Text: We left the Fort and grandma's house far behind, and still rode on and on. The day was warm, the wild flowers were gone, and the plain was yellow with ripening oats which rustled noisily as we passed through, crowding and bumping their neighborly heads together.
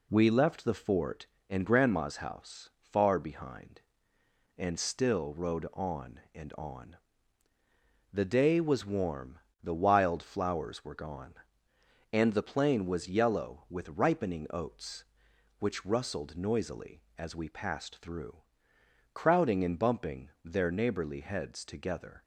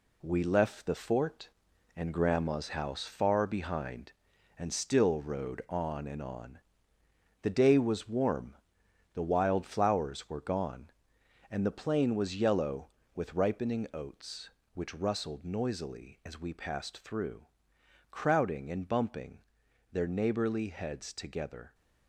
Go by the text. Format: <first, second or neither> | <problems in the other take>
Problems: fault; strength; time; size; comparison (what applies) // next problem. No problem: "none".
first | gets quieter; throughout; 7 dB // pauses between "bumping" and "their"; noticeable; at 19.4 s; 0.50 s long